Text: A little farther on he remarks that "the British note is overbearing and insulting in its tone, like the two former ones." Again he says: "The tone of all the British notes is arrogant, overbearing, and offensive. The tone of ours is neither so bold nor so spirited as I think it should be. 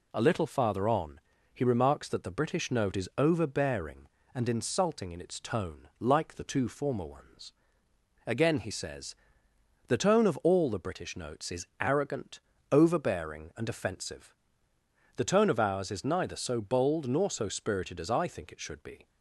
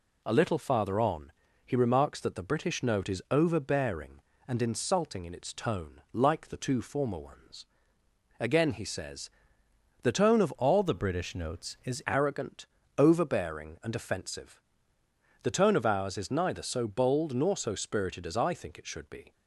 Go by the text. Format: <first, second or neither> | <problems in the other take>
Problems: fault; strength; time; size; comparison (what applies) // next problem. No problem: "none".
first | pauses between "on" and "he"; slight; at 1.3 s; 0.34 s long; slight in the first // changes voice from "all" to "is"; from 10.5 to 12.0 s; 1.5 s long